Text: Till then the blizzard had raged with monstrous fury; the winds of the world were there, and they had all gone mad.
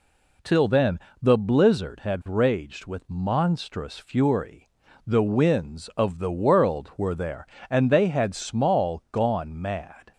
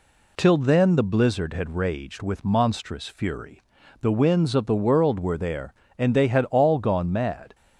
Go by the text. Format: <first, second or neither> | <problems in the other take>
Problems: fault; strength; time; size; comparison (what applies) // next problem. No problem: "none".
second | pauses between "then" and "the"; slight; at 0.9 s; 0.22 s long // says "small" for "all"; at 8.3 s